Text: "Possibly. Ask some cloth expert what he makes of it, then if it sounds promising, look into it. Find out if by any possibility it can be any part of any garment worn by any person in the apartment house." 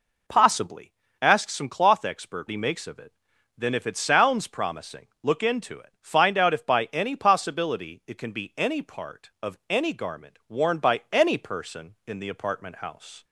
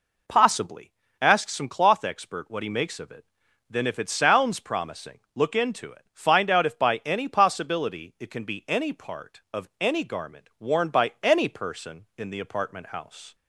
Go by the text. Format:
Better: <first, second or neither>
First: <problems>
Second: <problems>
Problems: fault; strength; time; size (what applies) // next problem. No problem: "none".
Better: second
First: skips "what"; at 2.4 s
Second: none